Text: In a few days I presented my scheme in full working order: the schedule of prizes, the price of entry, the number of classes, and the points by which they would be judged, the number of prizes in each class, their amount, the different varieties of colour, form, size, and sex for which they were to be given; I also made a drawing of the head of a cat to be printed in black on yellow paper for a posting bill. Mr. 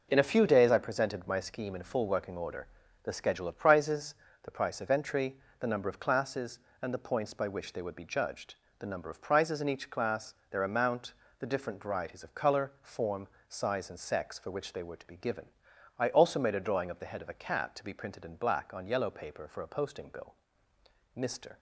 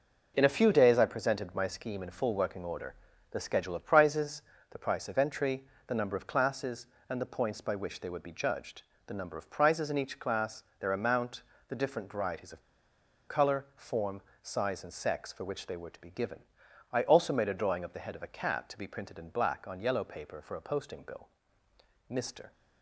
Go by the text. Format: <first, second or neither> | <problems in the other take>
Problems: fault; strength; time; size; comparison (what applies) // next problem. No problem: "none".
first | pauses between "of" and "colour"; noticeable; at 12.6 s; 0.67 s long